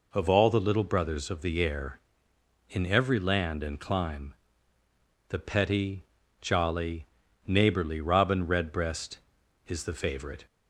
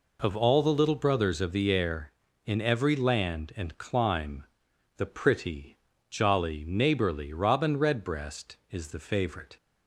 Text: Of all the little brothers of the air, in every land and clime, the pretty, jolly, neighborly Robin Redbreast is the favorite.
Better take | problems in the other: second | says "petty" for "pretty"; at 5.3 s

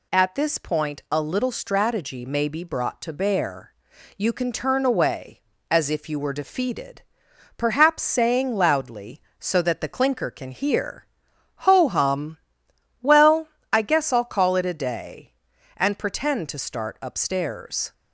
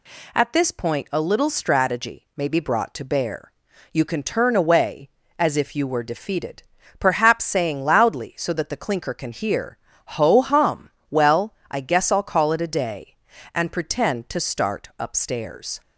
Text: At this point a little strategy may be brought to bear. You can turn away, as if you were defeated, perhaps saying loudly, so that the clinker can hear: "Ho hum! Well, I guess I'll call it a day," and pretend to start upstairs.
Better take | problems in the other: neither | none

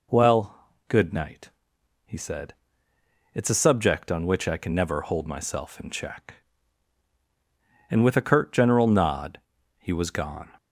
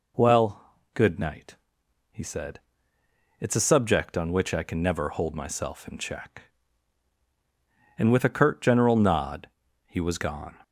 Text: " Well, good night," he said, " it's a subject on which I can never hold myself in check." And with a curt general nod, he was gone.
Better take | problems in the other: neither | none

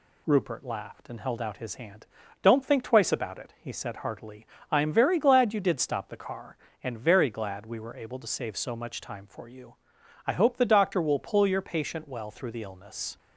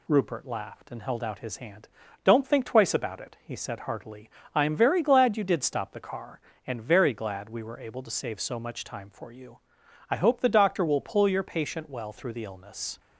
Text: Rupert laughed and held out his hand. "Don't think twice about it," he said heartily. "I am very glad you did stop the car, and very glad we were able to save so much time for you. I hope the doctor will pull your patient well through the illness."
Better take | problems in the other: neither | none

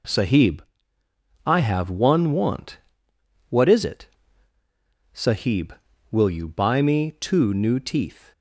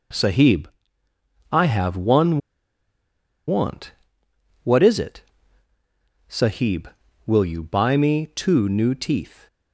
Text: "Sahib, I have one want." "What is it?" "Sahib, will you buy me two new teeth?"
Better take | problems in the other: first | pauses between "one" and "want"; at 2.3 s; 1.1 s long

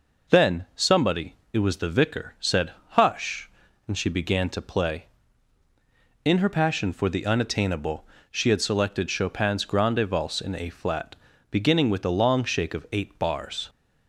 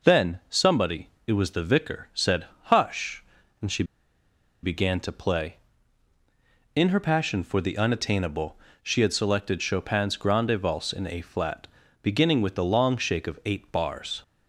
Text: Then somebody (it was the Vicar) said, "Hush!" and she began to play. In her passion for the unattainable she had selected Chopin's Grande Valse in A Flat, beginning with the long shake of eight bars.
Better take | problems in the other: first | pauses between "she" and "began"; noticeable; at 3.8 s; 0.79 s long // pauses between "unattainable" and "she"; slight; at 8.5 s; 0.24 s long; slight in the first

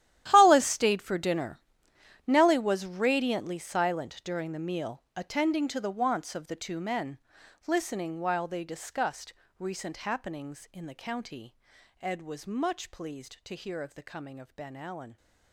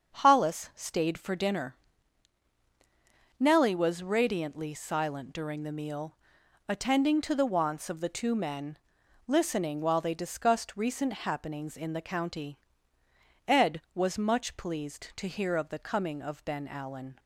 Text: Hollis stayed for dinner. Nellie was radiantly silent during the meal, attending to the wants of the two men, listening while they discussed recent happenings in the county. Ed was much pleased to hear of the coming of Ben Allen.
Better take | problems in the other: second | gets quieter; strong; throughout; 16 dB // starts louder than the rest; strong; until 1.3 s; 12.5 dB; also in the second // pauses between "discussed" and "recent"; slight; at 9.3 s; 0.24 s long

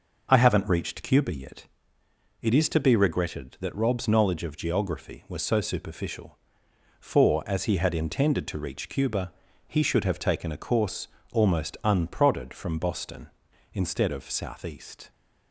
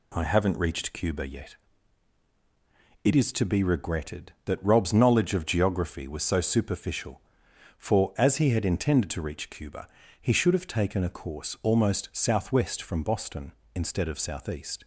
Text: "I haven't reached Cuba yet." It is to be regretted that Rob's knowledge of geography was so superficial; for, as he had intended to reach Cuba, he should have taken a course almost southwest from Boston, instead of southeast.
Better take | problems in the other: second | pauses between "course" and "almost"; slight; at 11.0 s; 0.24 s long // says "unprodded" for "southwest"; at 11.8 s

